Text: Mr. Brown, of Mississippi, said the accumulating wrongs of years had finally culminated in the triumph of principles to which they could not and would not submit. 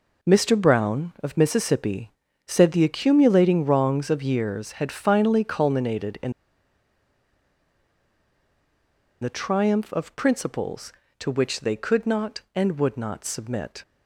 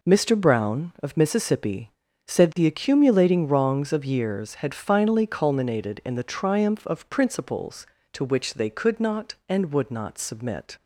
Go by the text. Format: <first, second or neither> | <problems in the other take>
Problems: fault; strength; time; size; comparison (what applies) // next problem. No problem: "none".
second | pauses between "in" and "the"; strong; at 6.3 s; 2.9 s long